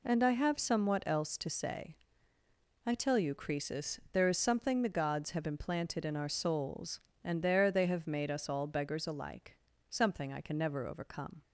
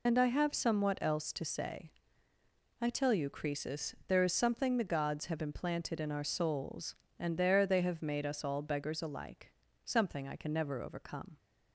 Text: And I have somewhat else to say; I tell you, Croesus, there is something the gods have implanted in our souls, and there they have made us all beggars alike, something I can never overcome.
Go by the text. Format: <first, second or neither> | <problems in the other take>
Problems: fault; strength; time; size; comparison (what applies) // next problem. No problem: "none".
first | loses the start of "And"; at 0.0 s; 60 ms